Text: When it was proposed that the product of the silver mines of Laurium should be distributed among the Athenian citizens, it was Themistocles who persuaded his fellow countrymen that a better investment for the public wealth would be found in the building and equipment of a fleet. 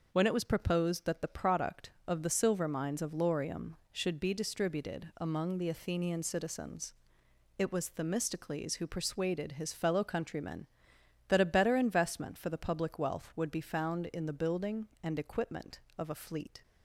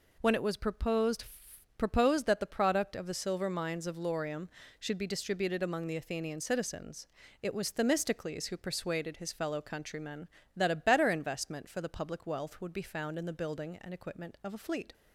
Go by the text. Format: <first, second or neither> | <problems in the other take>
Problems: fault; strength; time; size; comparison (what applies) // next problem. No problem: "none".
first | says "proposed" twice; at 1.7 s